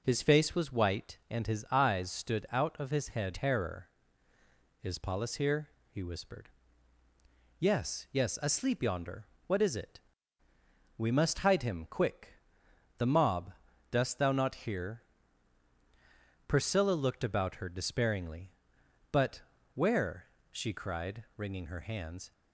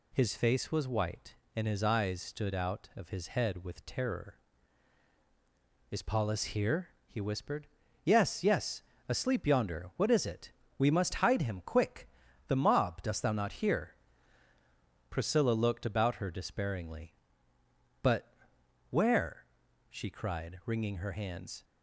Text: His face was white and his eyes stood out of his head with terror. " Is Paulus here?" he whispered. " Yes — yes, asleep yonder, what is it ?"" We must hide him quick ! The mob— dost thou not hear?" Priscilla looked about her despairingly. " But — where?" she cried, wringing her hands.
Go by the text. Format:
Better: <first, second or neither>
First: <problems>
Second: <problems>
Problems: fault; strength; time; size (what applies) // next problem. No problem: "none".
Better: second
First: starts louder than the rest; until 1.0 s; 6.5 dB // skips "with"; at 3.3 s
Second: none